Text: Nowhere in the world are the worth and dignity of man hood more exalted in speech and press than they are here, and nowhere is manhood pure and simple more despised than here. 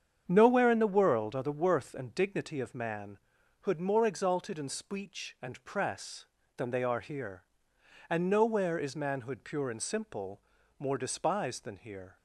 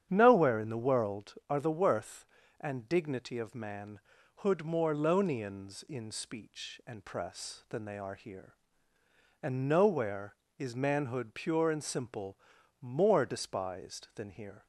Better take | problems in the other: first | starts louder than the rest; strong; until 1.1 s; 9 dB; strong in the first // pauses between "man" and "hood"; at 3.9 s; 0.38 s long; also in the first // says "lonians" for "exalted"; at 4.9 s // pauses between "simple" and "more"; at 12.3 s; 0.42 s long; also in the first

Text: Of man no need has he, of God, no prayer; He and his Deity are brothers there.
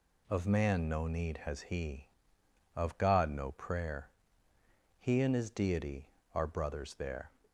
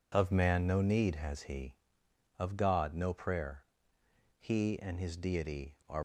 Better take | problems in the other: first | stops before "brothers there"; at 5.9 s

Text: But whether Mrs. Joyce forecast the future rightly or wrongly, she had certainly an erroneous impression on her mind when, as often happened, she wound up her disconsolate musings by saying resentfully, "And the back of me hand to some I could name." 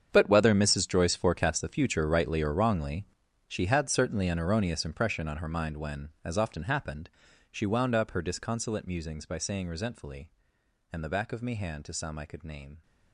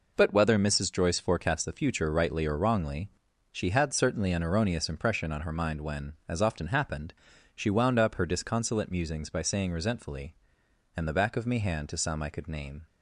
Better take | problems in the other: second | gets quieter; strong; throughout; 15 dB

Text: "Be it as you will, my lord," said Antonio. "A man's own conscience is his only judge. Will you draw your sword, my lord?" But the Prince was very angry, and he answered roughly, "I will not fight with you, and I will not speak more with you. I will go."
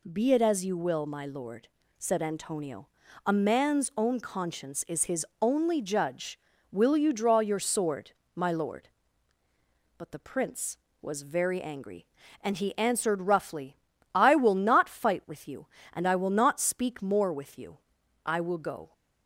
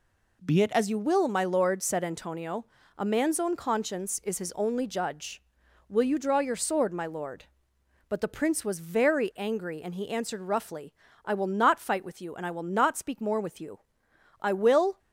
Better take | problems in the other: first | stops before "go"; at 14.9 s

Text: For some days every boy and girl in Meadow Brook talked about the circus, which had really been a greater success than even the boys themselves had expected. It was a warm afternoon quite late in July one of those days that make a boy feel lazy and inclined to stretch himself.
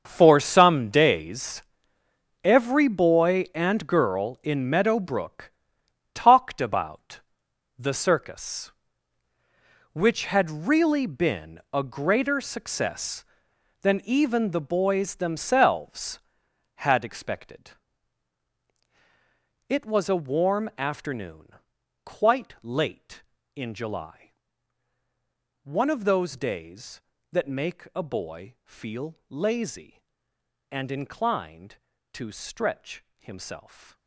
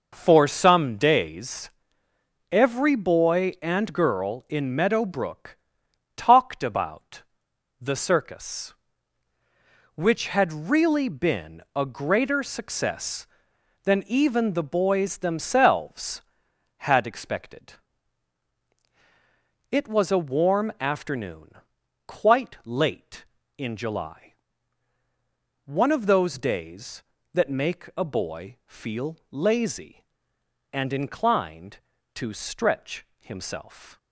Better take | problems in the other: second | gets quieter; strong; throughout; 13.5 dB // pauses between "days" and "every"; noticeable; at 1.6 s; 0.82 s long; noticeable in the second // pauses between "Brook" and "talked"; noticeable; at 5.5 s; 0.65 s long; noticeable in the second // pauses between "about" and "the"; noticeable; at 7.2 s; 0.56 s long; noticeable in the second // pauses between "afternoon" and "quite"; noticeable; at 21.5 s; 0.50 s long; noticeable in the second // pauses between "July" and "one"; strong; at 24.3 s; 1.3 s long; strong in the second

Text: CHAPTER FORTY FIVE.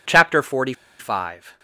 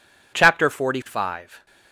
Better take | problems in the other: second | pauses between "FORTY" and "FIVE"; slight; at 0.7 s; 0.26 s long

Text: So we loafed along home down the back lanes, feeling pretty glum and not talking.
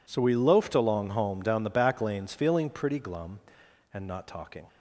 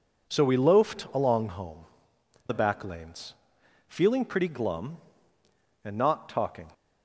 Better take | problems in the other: first | skips "down"; at 2.1 s

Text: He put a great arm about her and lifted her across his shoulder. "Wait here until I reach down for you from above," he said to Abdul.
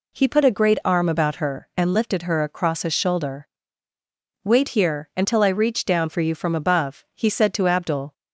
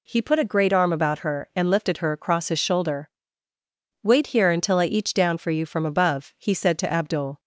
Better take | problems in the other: first | says "each" for "reach"; at 4.8 s

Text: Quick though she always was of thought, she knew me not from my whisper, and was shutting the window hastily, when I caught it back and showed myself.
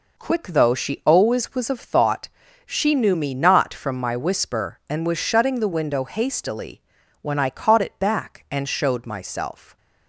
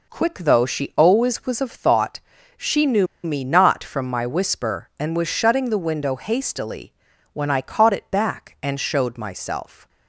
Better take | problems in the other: first | pauses between "knew" and "me"; slight; at 3.0 s; 0.17 s long

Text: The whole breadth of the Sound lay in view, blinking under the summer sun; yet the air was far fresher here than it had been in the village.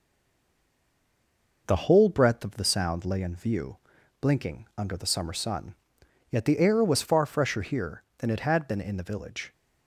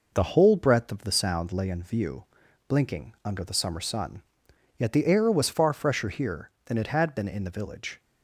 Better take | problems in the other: second | stays silent before the first word; noticeable; until 1.6 s; 1.6 s long

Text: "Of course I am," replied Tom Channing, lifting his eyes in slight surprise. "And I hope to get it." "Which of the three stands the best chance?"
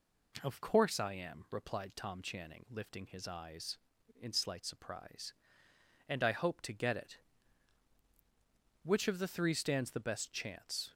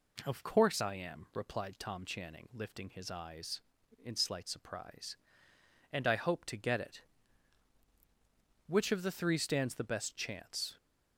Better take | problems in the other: neither | none

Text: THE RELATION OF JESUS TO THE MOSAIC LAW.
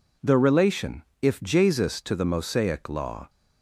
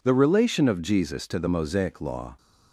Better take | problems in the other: second | says "If" for "OF"; at 1.2 s

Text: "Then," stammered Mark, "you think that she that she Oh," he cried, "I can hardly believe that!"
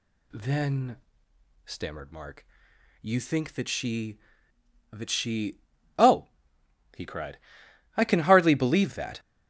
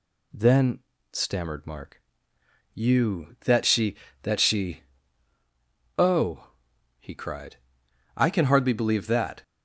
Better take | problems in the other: first | skips "think"; at 3.3 s // pauses between "she" and "Oh"; at 4.8 s; 1.1 s long; also in the first

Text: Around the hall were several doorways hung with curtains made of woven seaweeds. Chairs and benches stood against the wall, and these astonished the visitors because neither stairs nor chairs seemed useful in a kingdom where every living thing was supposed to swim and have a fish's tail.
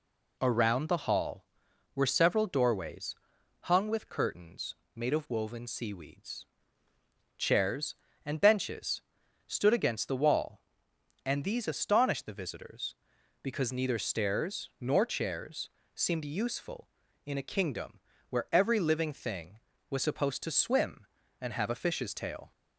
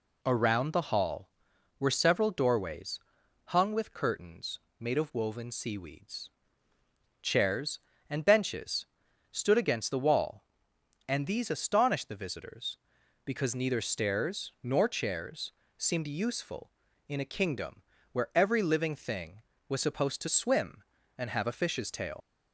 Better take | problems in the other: first | pauses between "doorways" and "hung"; noticeable; at 2.9 s; 0.46 s long; noticeable in the first // pauses between "curtains" and "made"; slight; at 4.5 s; 0.20 s long; slight in the first // pauses between "benches" and "stood"; noticeable; at 8.8 s; 0.46 s long; noticeable in the first // pauses between "chairs" and "seemed"; slight; at 15.5 s; 0.26 s long; slight in the first // pauses between "kingdom" and "where"; slight; at 17.8 s; 0.30 s long; slight in the first // leaves "tail" unfinished; at 22.2 s; 80 ms

